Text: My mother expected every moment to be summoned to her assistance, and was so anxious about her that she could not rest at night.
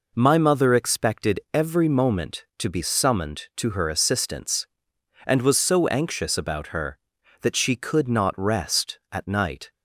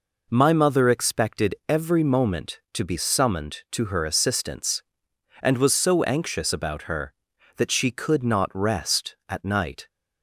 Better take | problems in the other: neither | none

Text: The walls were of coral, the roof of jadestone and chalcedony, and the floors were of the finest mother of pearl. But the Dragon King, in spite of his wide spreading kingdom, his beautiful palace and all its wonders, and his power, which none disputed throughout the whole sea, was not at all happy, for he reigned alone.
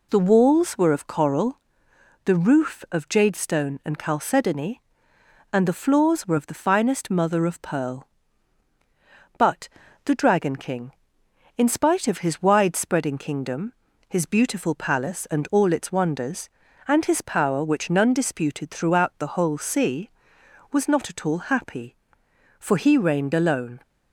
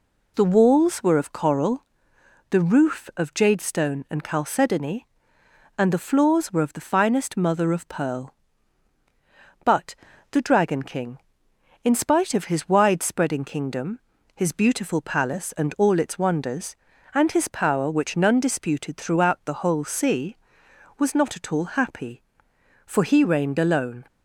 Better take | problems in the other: neither | pauses between "But" and "the"; slight; the same in both

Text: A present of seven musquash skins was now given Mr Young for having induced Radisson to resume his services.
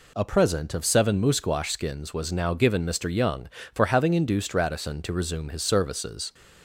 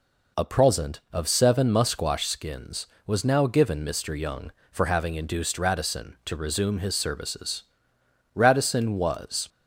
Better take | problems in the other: first | goes on to say "Radisson was"; noticeable; from 8.3 s on; 1.1 s long

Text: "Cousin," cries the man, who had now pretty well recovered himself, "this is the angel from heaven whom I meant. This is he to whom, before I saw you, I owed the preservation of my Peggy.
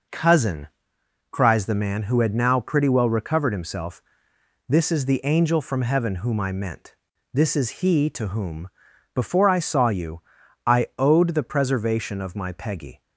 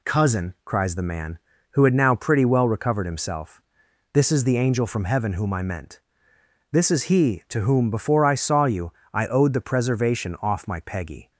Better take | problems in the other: first | says "off" for "of"; at 10.4 s

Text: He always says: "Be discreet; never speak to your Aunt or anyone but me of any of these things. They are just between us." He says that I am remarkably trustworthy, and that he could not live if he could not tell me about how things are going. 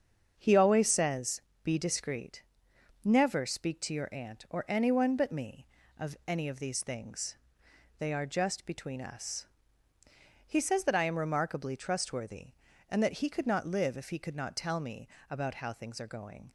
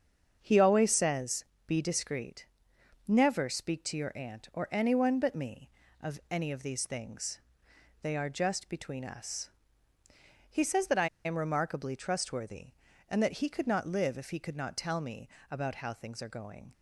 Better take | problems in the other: first | starts louder than the rest; strong; until 1.4 s; 7 dB; strong in the first // pauses between "I" and "am"; slight; at 11.0 s; 0.18 s long // pauses between "me" and "about"; slight; at 15.2 s; 0.22 s long; slight in the first

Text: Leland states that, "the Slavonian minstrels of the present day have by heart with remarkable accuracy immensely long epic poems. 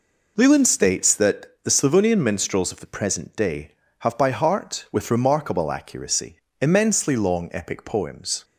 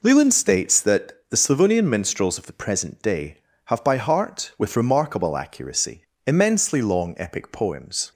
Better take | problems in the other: neither | pauses between "accuracy" and "immensely"; slight; the same in both

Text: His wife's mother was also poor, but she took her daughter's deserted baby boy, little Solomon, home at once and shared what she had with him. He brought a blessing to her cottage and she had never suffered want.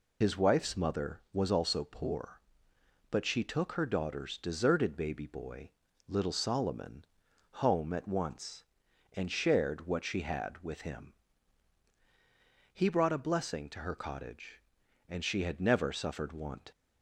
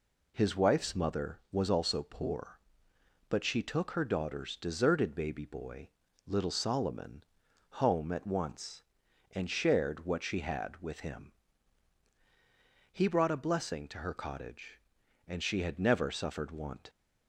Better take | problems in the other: second | loses the start of "His"; at 0.2 s; 80 ms

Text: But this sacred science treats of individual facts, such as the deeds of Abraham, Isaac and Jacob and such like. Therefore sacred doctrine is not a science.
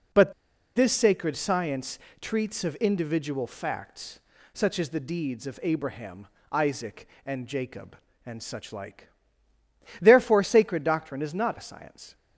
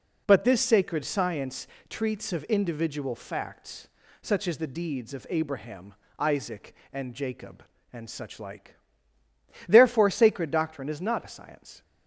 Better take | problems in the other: second | pauses between "But" and "this"; at 0.3 s; 0.43 s long // pauses between "science" and "treats"; slight; at 1.9 s; 0.22 s long; slight in the second

